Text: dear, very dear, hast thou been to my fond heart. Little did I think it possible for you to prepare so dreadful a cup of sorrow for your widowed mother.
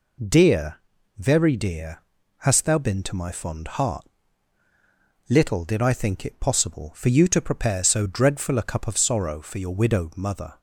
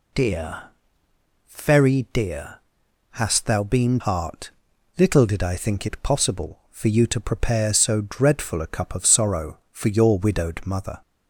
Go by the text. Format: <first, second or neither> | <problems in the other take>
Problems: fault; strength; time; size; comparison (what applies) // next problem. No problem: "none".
first | skips "to my fond"; at 3.9 s